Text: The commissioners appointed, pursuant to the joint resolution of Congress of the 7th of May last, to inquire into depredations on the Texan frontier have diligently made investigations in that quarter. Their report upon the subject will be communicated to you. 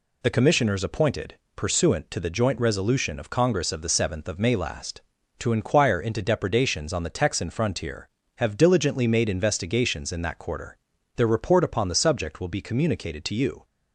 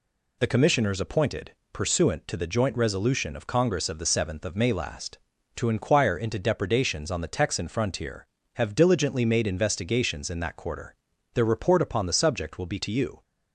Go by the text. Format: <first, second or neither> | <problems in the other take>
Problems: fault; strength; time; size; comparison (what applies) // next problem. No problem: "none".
first | skips "communicated"; at 12.7 s